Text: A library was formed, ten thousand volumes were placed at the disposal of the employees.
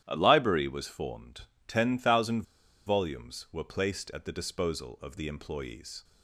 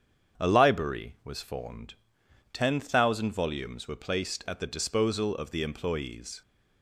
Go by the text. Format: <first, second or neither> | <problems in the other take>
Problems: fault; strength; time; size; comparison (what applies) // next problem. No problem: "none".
second | starts louder than the rest; strong; until 1.0 s; 11.5 dB; strong in the second // pauses between "thousand" and "volumes"; at 2.4 s; 0.43 s long